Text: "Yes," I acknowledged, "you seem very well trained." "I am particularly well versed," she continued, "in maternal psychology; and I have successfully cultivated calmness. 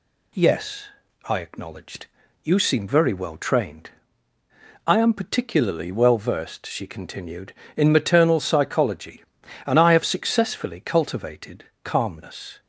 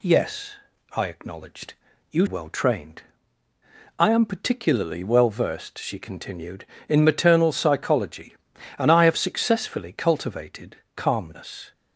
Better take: first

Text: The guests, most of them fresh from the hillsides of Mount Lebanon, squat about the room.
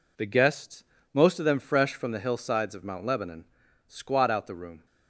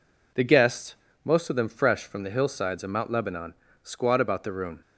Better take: second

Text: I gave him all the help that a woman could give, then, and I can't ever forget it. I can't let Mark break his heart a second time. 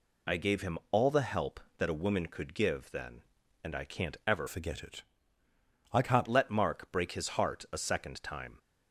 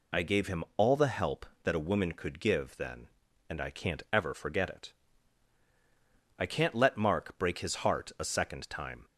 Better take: second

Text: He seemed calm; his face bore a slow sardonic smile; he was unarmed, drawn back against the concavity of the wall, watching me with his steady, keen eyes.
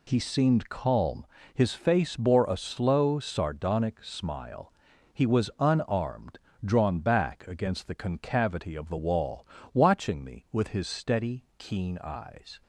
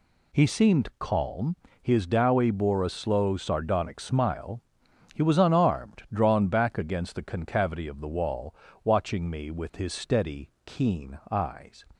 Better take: first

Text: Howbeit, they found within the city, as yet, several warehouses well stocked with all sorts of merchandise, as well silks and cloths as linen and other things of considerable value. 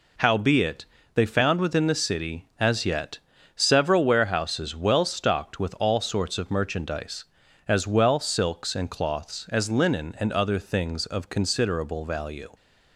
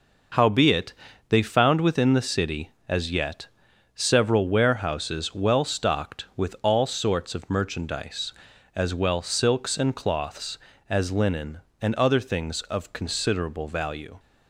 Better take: neither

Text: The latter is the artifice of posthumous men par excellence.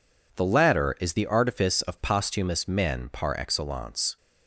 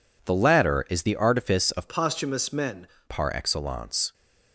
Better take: first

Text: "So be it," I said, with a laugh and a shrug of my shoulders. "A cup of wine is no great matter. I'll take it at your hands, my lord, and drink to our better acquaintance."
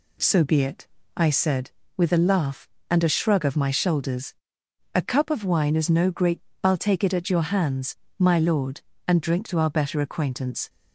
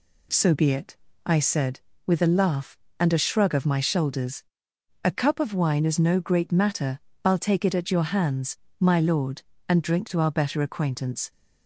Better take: second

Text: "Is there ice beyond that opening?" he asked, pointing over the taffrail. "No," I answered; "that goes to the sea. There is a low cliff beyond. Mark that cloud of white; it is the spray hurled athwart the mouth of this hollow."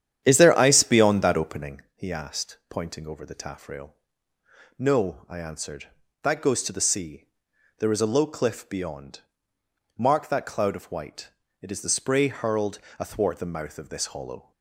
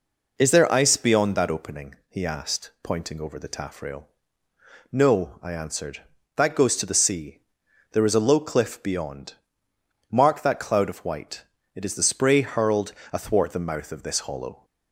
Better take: second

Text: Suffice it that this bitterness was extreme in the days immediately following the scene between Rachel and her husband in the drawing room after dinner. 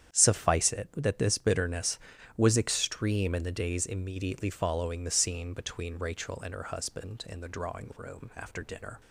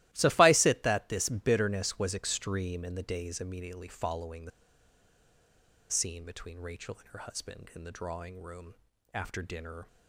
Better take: first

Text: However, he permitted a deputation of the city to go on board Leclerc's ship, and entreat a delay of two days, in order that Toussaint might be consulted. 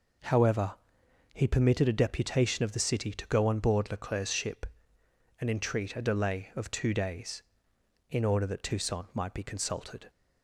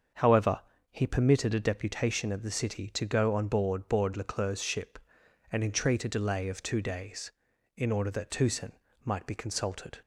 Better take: first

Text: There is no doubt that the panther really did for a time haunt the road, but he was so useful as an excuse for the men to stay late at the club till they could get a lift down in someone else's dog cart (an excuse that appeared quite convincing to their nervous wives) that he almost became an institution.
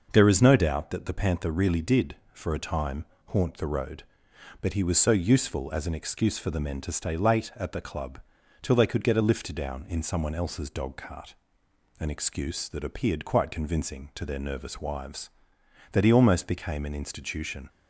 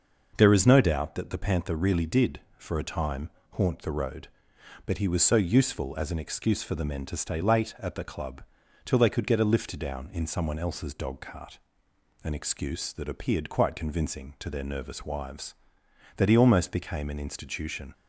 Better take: neither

